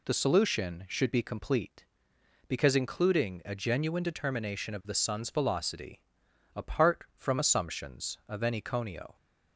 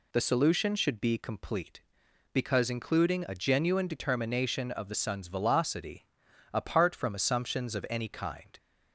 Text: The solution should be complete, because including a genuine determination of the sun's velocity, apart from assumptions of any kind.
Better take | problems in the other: second | says "conio" for "kind"; at 8.6 s

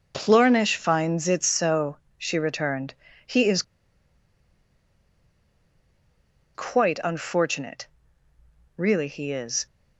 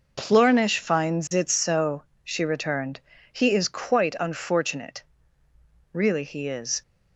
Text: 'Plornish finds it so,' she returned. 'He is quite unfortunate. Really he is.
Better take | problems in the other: second | pauses between "is" and "quite"; strong; at 3.6 s; 2.9 s long

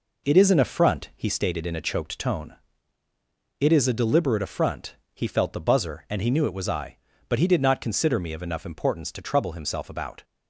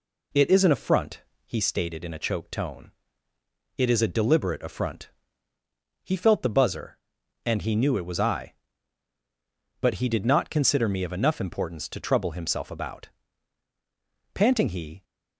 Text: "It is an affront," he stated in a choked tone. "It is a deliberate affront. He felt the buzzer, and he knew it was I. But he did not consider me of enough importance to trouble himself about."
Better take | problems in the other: first | goes on to say "Panting he"; noticeable; from 14.3 s on; 0.70 s long

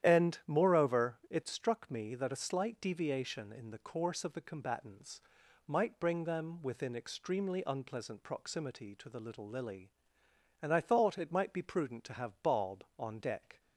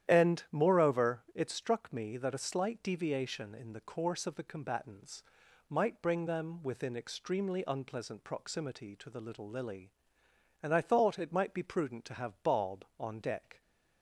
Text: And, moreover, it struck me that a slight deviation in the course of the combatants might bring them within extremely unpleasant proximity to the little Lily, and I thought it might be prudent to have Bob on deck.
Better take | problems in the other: neither | starts louder than the rest; strong; the same in both // pauses between "combatants" and "might"; the same in both

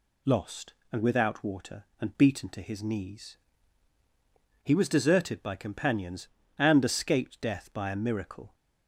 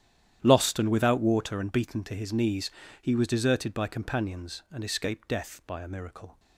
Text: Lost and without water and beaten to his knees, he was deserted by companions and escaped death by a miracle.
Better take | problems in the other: first | starts louder than the rest; strong; until 1.7 s; 10.5 dB

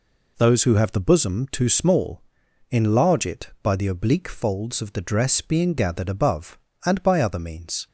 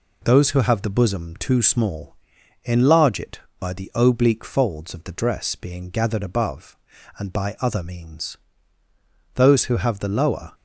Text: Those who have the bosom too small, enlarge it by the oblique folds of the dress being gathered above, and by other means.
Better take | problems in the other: first | goes on to say "Those who have the lower"; noticeable; from 9.3 s on; 1.1 s long

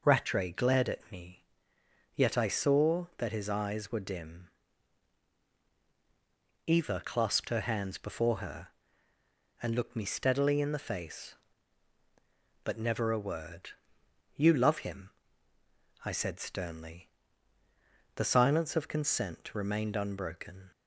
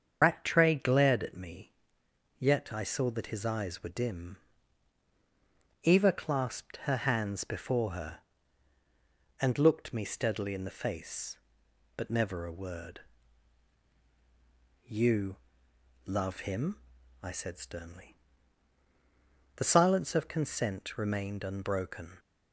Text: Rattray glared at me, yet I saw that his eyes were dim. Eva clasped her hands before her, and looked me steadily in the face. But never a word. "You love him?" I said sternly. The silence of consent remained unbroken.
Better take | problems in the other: first | loses the start of "Rattray"; at 0.2 s; 90 ms // starts louder than the rest; strong; until 1.2 s; 7 dB // pauses between "You" and "love"; noticeable; at 15.3 s; 0.68 s long

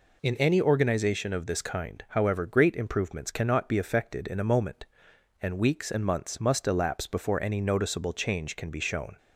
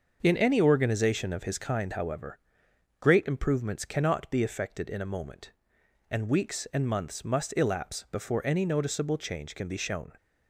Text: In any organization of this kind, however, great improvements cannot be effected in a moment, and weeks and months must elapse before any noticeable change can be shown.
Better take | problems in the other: first | starts louder than the rest; until 1.2 s; 6.5 dB // says "his" for "this"; at 1.4 s

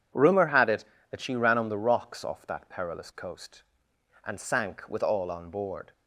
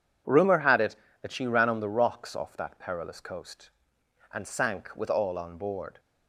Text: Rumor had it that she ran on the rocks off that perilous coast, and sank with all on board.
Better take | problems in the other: neither | none

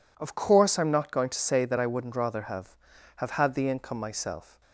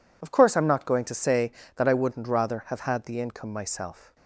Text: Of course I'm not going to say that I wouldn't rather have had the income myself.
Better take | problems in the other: second | says "have" twice; at 3.1 s

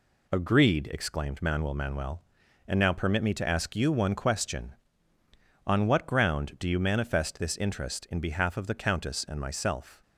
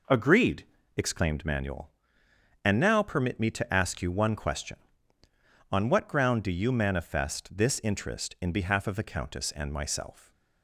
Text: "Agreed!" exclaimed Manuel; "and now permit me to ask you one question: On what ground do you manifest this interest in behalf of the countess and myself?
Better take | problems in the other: second | says "Manuel" twice; at 1.7 s

